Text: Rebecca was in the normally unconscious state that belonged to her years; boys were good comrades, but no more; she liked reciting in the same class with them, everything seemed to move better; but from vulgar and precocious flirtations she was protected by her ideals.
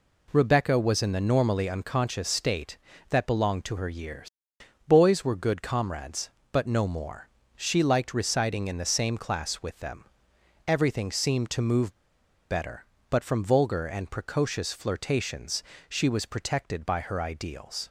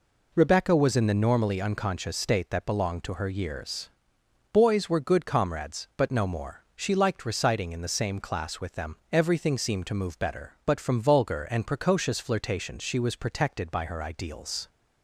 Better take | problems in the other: second | pauses between "move" and "better"; noticeable; at 11.9 s; 0.55 s long // pauses between "flirtations" and "she"; slight; at 15.6 s; 0.24 s long

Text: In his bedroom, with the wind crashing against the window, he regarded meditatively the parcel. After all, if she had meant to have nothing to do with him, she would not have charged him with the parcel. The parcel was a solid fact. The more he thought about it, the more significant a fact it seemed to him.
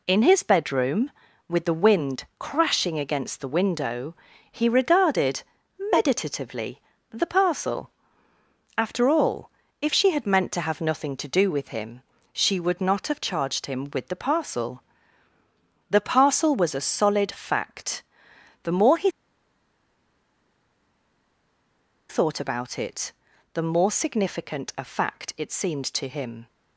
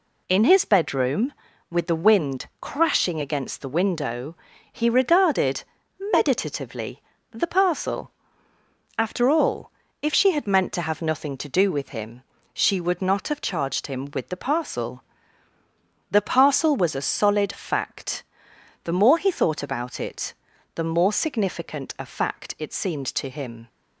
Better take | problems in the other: second | pauses between "regarded" and "meditatively"; noticeable; at 5.4 s; 0.50 s long; noticeable in the second // pauses between "meditatively" and "the"; slight; at 6.8 s; 0.30 s long; slight in the second // pauses between "he" and "thought"; strong; at 19.1 s; 2.9 s long

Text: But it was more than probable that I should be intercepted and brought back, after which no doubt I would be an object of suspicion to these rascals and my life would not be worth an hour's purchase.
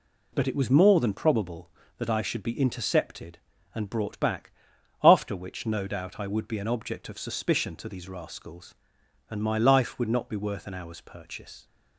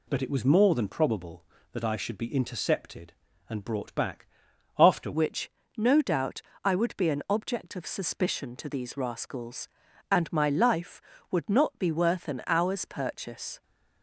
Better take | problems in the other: first | changes voice at "which"; from 5.1 s on; 8.5 s long // pauses between "which" and "no"; slight; at 5.4 s; 0.28 s long // pauses between "doubt" and "I"; slight; at 6.4 s; 0.22 s long

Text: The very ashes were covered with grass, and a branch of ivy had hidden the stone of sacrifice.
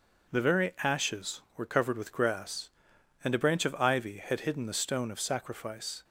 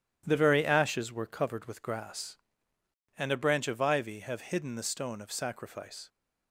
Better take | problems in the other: first | starts louder than the rest; strong; until 1.2 s; 11 dB // says "have" for "had"; at 4.2 s

